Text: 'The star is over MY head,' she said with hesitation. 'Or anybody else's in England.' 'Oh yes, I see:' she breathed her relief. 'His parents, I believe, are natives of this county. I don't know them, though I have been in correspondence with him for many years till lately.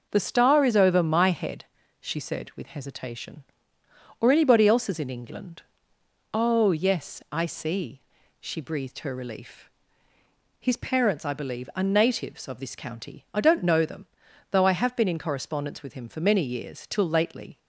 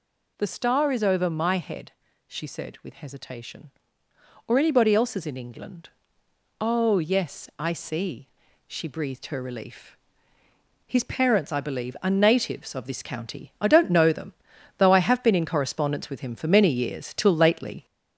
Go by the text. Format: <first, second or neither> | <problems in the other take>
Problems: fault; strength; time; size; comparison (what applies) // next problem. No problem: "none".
first | gets louder; slight; throughout; 3.5 dB